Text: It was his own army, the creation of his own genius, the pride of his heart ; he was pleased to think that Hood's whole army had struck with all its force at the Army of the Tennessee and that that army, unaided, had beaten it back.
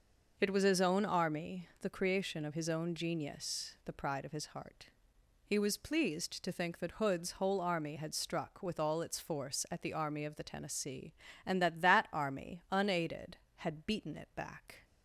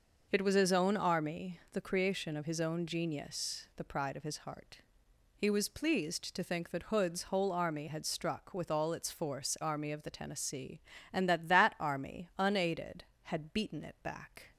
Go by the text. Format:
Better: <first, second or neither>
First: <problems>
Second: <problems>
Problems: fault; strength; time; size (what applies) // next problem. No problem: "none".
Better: first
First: none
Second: skips "at the"; at 9.5 s